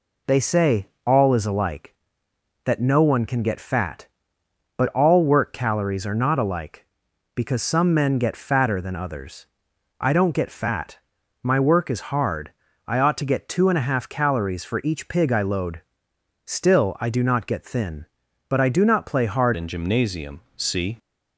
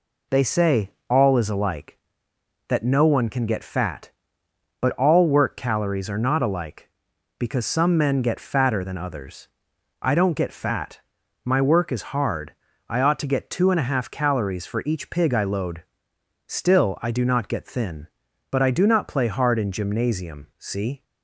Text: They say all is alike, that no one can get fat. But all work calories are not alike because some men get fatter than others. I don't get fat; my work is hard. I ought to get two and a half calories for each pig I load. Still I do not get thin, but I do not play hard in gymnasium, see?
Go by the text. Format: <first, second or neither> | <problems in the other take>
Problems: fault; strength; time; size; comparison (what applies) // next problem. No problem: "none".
second | pauses between "say" and "all"; slight; at 0.8 s; 0.18 s long; slight in the second // changes voice at "in"; from 19.5 s on; 1.4 s long